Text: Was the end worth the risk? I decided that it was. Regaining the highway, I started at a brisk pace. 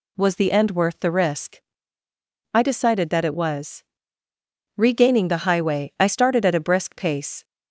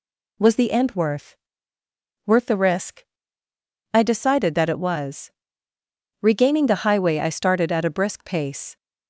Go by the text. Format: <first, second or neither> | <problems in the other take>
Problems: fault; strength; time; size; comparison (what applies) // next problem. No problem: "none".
first | says "worth" twice; at 2.2 s